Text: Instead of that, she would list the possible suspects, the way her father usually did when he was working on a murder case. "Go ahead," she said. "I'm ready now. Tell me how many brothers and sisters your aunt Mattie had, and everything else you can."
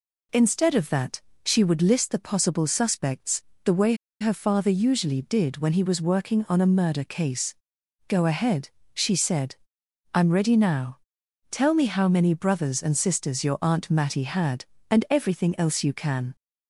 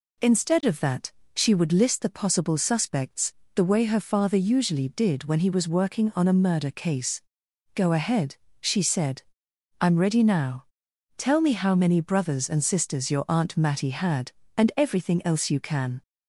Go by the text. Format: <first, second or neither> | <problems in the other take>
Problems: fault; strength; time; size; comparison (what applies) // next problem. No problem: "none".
second | pauses between "way" and "her"; slight; at 3.9 s; 0.25 s long